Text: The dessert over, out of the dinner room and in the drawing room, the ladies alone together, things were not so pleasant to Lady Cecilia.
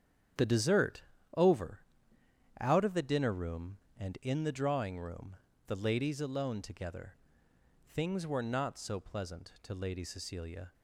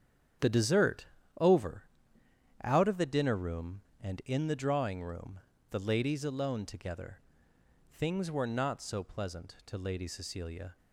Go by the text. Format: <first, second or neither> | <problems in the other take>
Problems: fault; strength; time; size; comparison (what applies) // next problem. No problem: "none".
neither | starts louder than the rest; strong; the same in both // pauses between "dessert" and "over"; slight; the same in both